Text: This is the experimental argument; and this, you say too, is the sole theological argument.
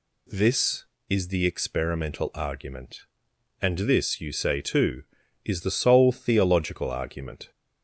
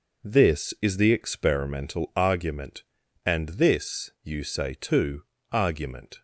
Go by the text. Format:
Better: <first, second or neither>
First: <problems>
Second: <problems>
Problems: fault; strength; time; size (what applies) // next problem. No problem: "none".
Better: first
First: none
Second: skips "is the sole theological"; at 5.3 s